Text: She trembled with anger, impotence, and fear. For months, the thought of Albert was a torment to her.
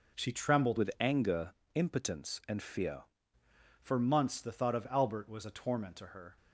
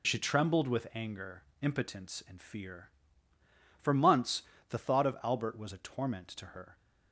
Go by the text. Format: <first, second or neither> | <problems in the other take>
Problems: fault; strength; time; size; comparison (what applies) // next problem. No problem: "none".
second | changes voice from "with" to "fear"; from 0.7 to 3.0 s; 2.3 s long